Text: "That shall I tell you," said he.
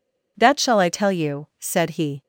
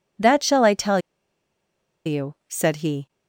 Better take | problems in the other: first | pauses between "tell" and "you"; at 0.9 s; 1.0 s long

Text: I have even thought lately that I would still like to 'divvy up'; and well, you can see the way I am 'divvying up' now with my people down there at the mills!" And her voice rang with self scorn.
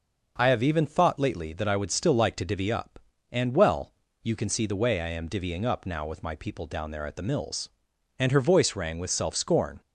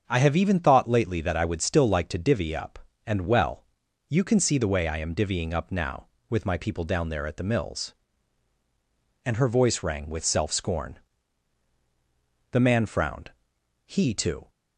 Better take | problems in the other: first | starts louder than the rest; until 1.0 s; 7 dB; noticeable in the first // goes on to say "The man frowned He too"; strong; from 12.5 s on; 1.9 s long

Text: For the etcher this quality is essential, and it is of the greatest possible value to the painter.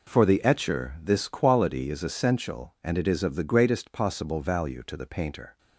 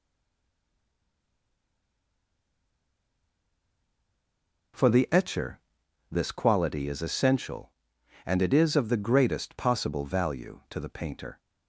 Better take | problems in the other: first | stays silent before the first word; strong; until 4.7 s; 4.7 s long // pauses between "etcher" and "this"; noticeable; at 5.6 s; 0.50 s long

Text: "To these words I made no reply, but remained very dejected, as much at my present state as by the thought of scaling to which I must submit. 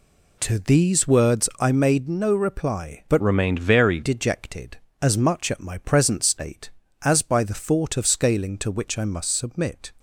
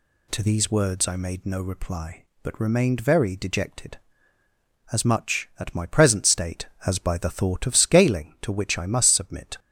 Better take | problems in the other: second | changes voice from "remained" to "very"; from 3.2 to 4.0 s; 0.8 s long

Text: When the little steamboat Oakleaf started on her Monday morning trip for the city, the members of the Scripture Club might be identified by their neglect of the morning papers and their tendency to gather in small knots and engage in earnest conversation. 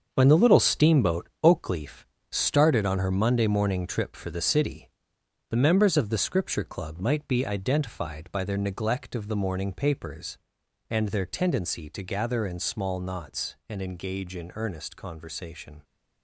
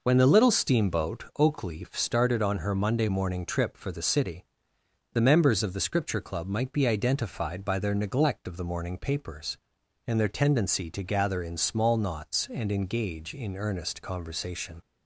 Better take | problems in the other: second | gets quieter; strong; throughout; 9.5 dB // pauses between "Oakleaf" and "started"; slight; at 2.0 s; 0.26 s long

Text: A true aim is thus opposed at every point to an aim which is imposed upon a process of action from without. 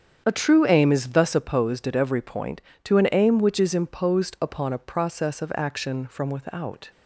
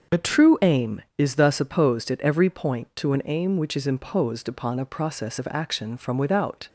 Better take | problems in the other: neither | starts louder than the rest; the same in both

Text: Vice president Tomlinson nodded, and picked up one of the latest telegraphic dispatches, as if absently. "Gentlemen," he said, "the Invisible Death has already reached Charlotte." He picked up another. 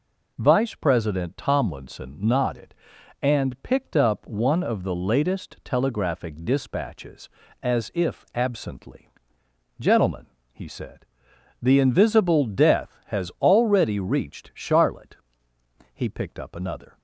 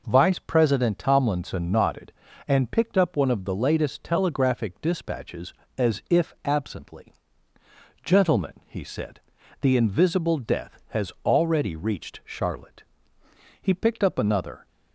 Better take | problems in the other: neither | none

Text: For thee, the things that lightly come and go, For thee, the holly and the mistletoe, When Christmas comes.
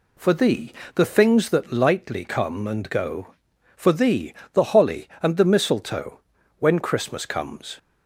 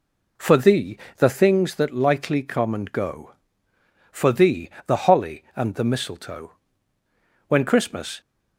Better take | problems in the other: first | stops before "comes"; at 8.2 s

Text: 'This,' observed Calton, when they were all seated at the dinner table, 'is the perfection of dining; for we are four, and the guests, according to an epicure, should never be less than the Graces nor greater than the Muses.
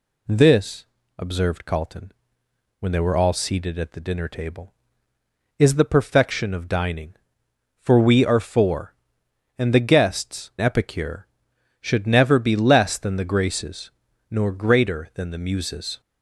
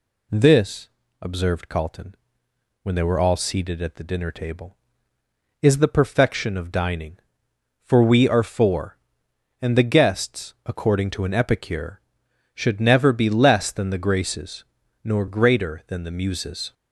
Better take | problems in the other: second | skips "according to an"; at 10.5 s // pauses between "Graces" and "nor"; at 13.9 s; 0.38 s long; also in the second

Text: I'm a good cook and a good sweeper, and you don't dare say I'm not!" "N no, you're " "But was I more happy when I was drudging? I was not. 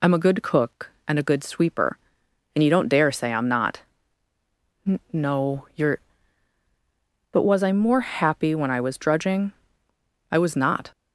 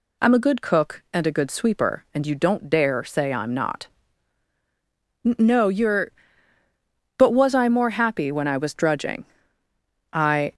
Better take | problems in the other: first | stops before "was not"; at 10.5 s

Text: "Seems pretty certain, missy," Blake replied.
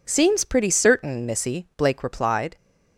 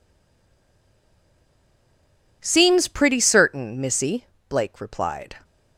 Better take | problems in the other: first | stays silent before the first word; until 2.4 s; 2.4 s long

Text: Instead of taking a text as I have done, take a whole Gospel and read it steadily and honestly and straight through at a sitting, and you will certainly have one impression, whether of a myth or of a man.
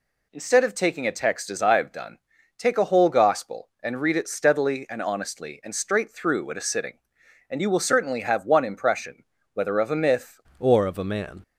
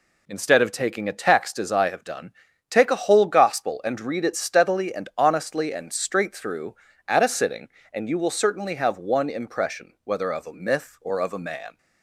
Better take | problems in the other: second | changes voice at "or"; from 10.5 s on; 0.9 s long

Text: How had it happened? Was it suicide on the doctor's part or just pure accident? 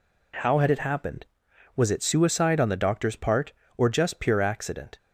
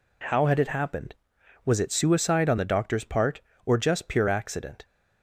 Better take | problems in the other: neither | none

